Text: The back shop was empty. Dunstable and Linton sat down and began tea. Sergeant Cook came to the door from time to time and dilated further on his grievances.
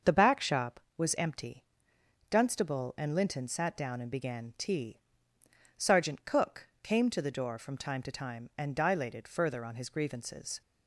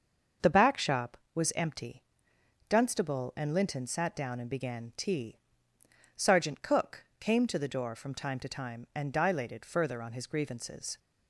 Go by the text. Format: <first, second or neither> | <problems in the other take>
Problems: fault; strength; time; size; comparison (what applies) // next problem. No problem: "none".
neither | starts louder than the rest; the same in both // pauses between "Cook" and "came"; slight; the same in both